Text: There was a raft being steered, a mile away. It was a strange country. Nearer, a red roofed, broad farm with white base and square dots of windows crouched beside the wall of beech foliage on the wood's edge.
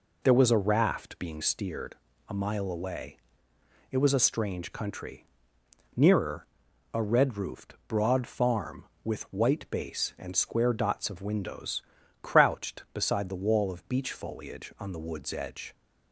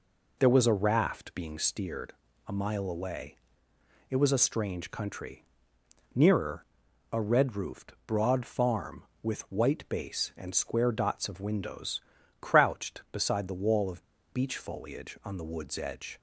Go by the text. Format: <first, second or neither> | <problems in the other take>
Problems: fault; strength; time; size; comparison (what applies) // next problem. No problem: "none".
first | pauses between "windows" and "crouched"; at 11.9 s; 0.40 s long; also in the first // pauses between "of" and "beech"; slight; at 14.0 s; 0.26 s long